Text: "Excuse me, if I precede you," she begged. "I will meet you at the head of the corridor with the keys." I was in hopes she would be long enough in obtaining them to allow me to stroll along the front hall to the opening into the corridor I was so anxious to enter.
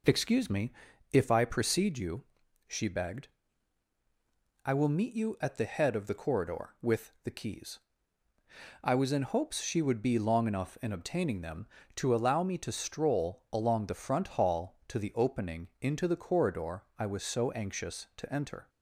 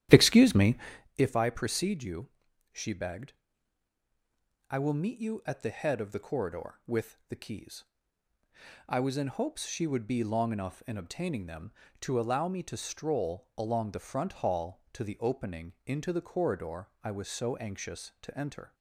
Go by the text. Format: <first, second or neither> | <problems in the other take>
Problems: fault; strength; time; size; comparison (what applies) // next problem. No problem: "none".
first | starts louder than the rest; strong; until 1.1 s; 12 dB // pauses between "corridor" and "I"; slight; at 16.8 s; 0.16 s long; slight in the first